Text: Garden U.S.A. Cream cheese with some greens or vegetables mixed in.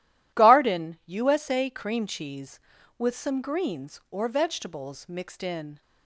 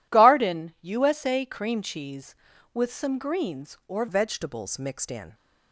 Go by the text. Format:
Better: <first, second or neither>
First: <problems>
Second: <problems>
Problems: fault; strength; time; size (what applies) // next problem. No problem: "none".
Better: first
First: none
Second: changes voice at "vegetables"; from 4.0 s on; 1.3 s long